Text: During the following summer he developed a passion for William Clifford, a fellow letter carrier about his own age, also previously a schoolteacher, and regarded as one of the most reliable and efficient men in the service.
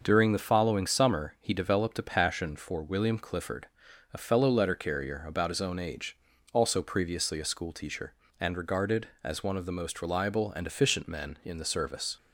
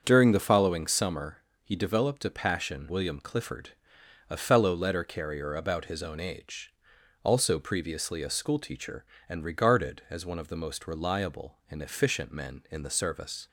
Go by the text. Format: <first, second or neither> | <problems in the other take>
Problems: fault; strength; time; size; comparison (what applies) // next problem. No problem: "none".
first | starts louder than the rest; until 1.0 s; 7 dB; also in the first // pauses between "summer" and "he"; slight; at 1.3 s; 0.24 s long // skips "for"; at 2.8 s